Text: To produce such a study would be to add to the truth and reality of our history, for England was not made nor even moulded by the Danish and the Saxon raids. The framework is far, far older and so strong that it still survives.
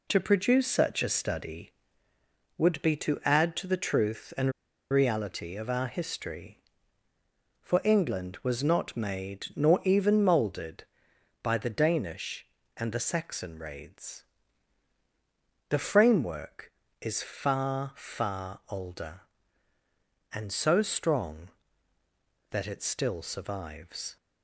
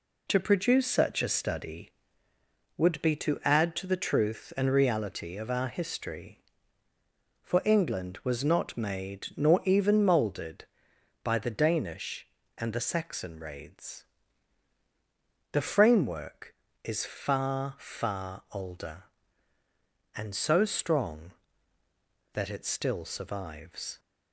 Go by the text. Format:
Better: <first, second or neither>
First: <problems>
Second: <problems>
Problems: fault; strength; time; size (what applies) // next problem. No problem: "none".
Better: second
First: pauses between "and" and "reality"; at 4.5 s; 0.39 s long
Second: none